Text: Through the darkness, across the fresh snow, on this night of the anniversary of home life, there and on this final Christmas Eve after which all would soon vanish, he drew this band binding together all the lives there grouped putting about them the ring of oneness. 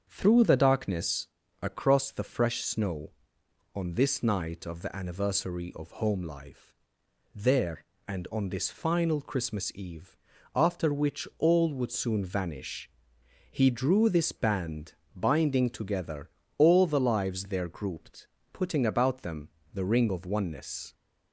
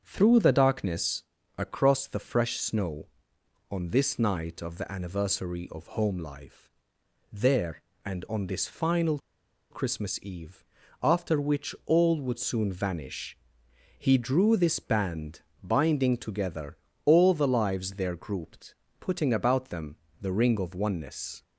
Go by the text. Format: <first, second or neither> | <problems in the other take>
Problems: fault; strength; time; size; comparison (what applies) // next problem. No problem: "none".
first | starts louder than the rest; strong; until 1.0 s; 7 dB; also in the first // pauses between "final" and "Christmas"; noticeable; at 9.1 s; 0.52 s long // pauses between "Eve" and "after"; at 10.6 s; 0.38 s long; also in the first // pauses between "band" and "binding"; slight; at 15.4 s; 0.20 s long; slight in the first // pauses between "together" and "all"; slight; at 16.7 s; 0.26 s long; slight in the first // pauses between "grouped" and "putting"; slight; at 18.7 s; 0.26 s long; slight in the first // pauses between "them" and "the"; slight; at 19.9 s; 0.26 s long; slight in the first